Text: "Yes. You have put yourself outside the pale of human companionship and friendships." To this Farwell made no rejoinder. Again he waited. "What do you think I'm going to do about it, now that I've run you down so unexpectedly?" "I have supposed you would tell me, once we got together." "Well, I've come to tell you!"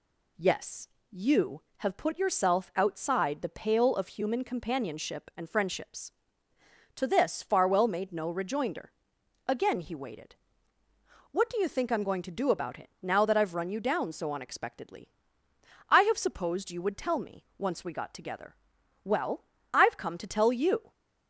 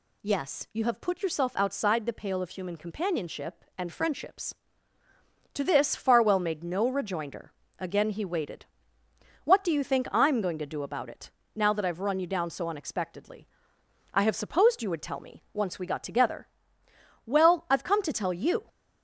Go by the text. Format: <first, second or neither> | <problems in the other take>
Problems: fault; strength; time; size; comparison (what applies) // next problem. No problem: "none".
neither | none